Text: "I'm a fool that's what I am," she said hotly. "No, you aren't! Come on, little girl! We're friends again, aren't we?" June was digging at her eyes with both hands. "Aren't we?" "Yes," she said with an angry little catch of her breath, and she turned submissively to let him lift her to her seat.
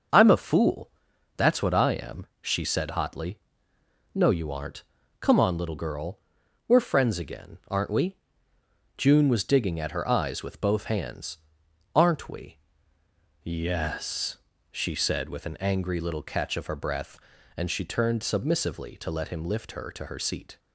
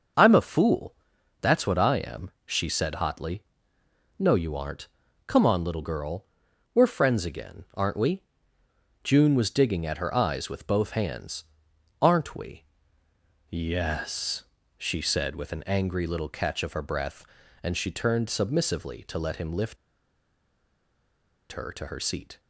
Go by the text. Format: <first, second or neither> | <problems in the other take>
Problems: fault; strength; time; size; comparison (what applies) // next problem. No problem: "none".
first | starts louder than the rest; until 1.6 s; 6.5 dB; also in the first // pauses between "fool" and "that's"; noticeable; at 0.9 s; 0.46 s long; noticeable in the first // pauses between "lift" and "her"; strong; at 19.7 s; 1.7 s long